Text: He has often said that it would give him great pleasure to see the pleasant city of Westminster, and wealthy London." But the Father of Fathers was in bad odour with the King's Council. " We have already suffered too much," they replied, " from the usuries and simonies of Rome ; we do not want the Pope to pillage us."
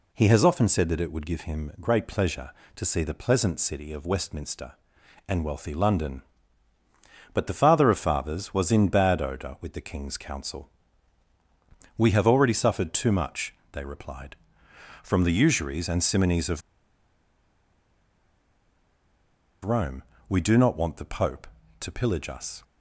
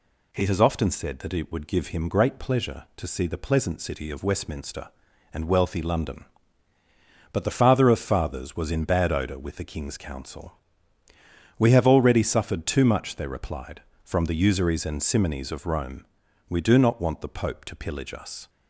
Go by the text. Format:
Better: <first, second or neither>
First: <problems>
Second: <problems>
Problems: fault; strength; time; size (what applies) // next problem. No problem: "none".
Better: second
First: pauses between "of" and "Rome"; strong; at 16.6 s; 3.0 s long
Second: none